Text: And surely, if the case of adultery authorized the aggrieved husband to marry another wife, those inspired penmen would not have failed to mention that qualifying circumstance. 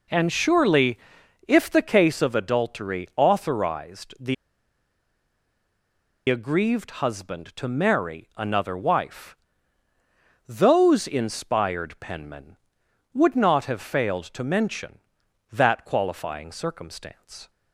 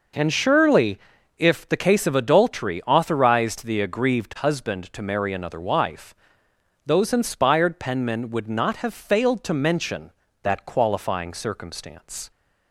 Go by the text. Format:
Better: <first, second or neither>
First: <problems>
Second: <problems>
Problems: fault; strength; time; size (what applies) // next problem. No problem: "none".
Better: second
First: pauses between "the" and "aggrieved"; strong; at 4.3 s; 1.9 s long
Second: none